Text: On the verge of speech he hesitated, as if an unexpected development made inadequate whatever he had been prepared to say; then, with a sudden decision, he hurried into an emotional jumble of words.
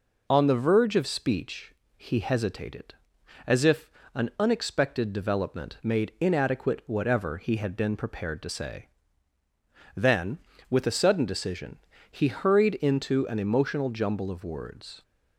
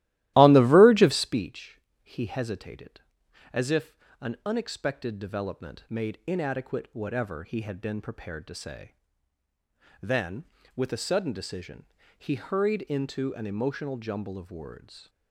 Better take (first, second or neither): first